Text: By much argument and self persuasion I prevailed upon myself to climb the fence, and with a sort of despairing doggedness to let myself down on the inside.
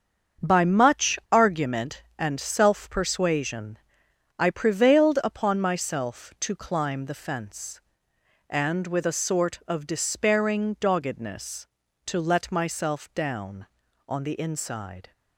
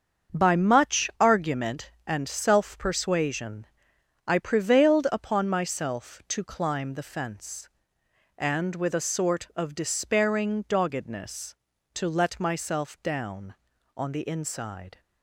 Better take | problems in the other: neither | starts louder than the rest; the same in both // pauses between "persuasion" and "I"; noticeable; the same in both

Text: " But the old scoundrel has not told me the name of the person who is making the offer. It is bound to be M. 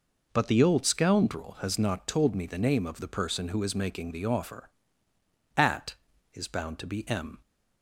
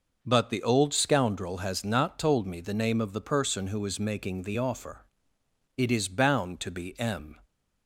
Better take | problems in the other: second | says "At" for "It"; at 5.5 s

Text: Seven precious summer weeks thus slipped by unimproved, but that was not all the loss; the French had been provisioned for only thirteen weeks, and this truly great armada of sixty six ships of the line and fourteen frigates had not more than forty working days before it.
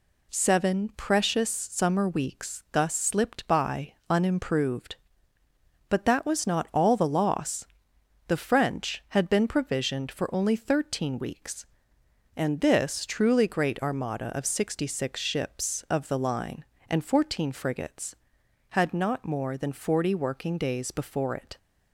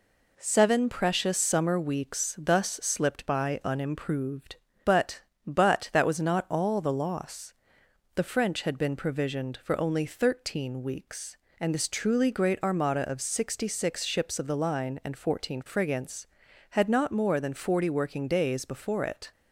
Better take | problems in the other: first | says "but" twice; at 5.4 s

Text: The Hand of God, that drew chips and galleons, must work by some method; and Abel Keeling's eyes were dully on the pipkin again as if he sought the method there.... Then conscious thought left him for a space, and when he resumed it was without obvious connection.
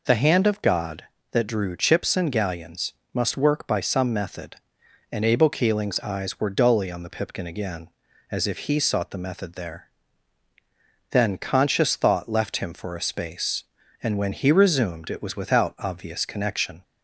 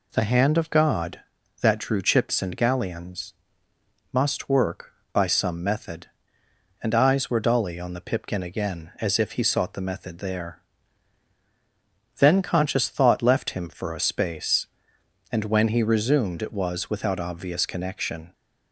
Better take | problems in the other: first | skips "Abel Keeling's"; at 6.9 s

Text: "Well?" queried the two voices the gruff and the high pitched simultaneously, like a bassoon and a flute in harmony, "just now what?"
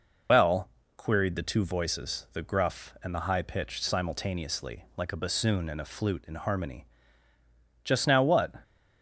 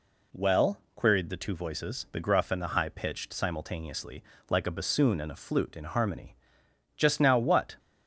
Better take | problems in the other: second | loses the start of "Well"; at 0.2 s; 75 ms

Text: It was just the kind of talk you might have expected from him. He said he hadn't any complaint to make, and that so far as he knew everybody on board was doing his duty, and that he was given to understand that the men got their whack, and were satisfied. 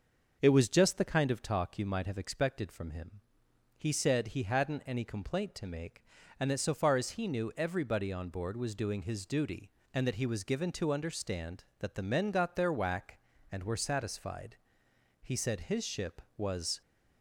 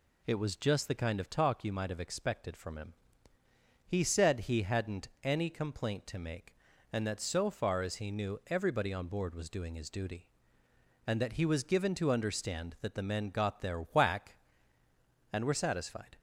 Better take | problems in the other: second | goes on to say "He said his ship was"; from 15.2 s on; 1.6 s long

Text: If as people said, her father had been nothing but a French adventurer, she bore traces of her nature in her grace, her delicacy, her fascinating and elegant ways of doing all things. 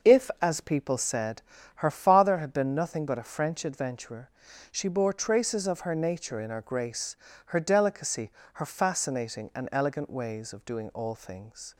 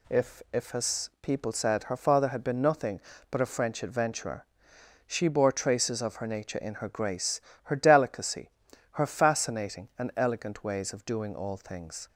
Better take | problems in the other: first | says "If" twice; at 0.5 s

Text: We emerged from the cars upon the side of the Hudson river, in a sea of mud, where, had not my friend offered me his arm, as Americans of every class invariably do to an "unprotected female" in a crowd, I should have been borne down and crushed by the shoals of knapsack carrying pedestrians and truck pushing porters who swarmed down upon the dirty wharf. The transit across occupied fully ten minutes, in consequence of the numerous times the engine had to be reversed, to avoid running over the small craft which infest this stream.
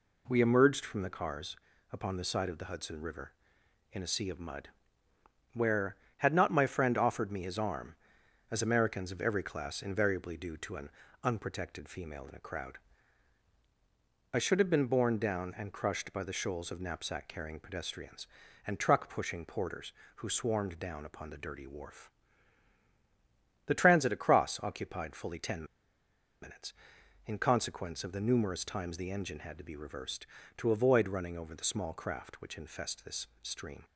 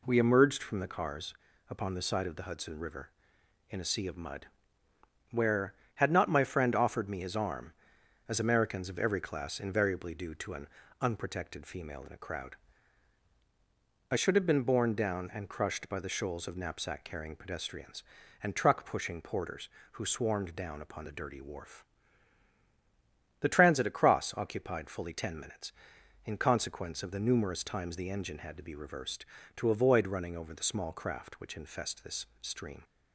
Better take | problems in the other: second | pauses between "cars" and "upon"; at 1.5 s; 0.38 s long; also in the second // pauses between "an" and "unprotected"; slight; at 10.9 s; 0.32 s long; slight in the second // pauses between "ten" and "minutes"; noticeable; at 25.6 s; 0.77 s long

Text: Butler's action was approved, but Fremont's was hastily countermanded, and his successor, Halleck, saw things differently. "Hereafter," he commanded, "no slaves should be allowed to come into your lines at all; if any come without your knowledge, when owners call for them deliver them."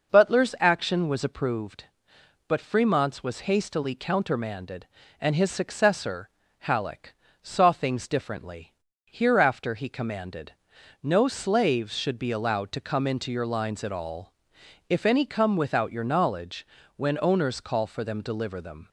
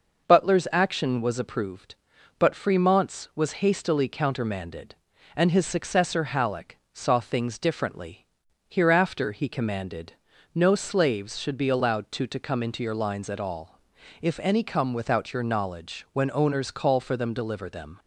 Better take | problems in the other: first | says "to" twice; at 12.2 s

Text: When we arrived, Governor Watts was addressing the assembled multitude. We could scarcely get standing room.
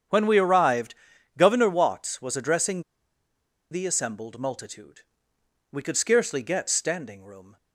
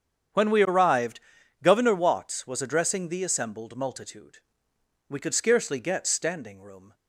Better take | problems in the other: second | starts louder than the rest; strong; until 1.5 s; 8 dB; strong in the second // pauses between "addressing" and "the"; noticeable; at 2.8 s; 0.88 s long

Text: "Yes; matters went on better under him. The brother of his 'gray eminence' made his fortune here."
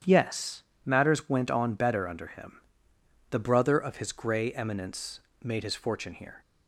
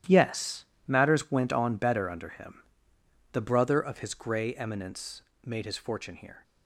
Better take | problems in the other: first | gets quieter; strong; throughout; 12 dB // starts louder than the rest; strong; until 1.2 s; 11.5 dB; strong in the first // pauses between "eminence" and "made"; slight; at 5.2 s; 0.20 s long; slight in the first

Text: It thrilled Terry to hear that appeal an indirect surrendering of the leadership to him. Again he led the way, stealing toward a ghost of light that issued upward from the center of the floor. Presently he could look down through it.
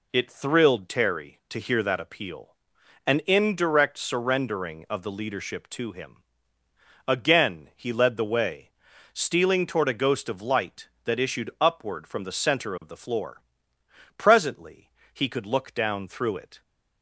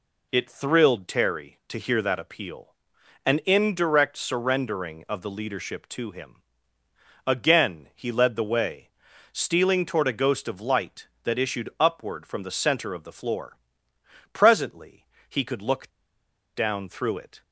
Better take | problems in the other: first | pauses between "appeal" and "an"; noticeable; at 2.7 s; 0.52 s long; noticeable in the first // pauses between "Presently" and "he"; slight; at 15.0 s; 0.24 s long; slight in the first // pauses between "look" and "down"; noticeable; at 15.9 s; 0.65 s long

